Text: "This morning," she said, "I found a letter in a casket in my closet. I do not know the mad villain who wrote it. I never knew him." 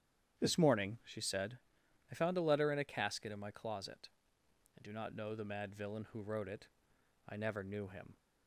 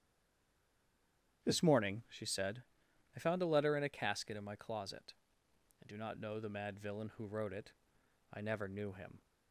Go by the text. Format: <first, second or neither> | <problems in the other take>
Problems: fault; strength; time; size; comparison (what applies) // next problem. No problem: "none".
first | stays silent before the first word; noticeable; until 1.4 s; 1.4 s long // starts louder than the rest; strong; until 2.4 s; 9.5 dB; strong in the first